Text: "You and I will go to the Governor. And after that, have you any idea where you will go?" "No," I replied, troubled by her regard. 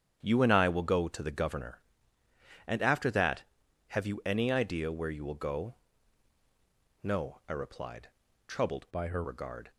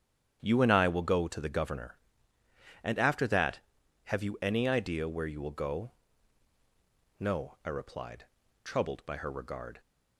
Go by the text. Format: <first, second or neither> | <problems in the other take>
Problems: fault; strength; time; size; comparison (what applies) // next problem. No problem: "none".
second | starts louder than the rest; strong; until 1.2 s; 9 dB; strong in the second // changes voice from "by" to "her"; from 8.9 to 9.2 s; 0.3 s long